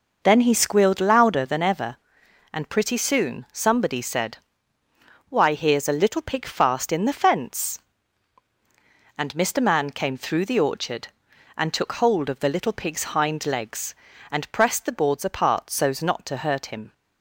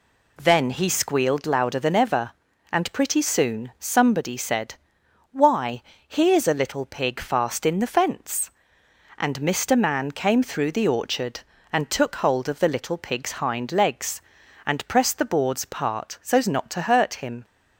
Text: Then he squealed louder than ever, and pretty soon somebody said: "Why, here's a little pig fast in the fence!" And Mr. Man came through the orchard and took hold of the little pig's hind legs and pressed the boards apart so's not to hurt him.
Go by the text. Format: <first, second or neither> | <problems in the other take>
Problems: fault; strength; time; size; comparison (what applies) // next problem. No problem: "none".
neither | none